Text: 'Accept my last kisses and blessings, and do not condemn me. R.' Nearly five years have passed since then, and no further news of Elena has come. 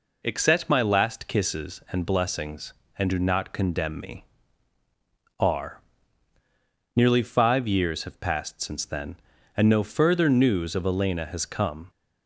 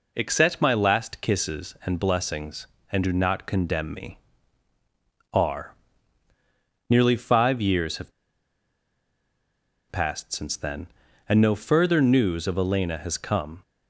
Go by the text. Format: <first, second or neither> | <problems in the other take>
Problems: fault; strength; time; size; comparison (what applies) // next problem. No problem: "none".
first | pauses between "have" and "passed"; strong; at 8.1 s; 1.7 s long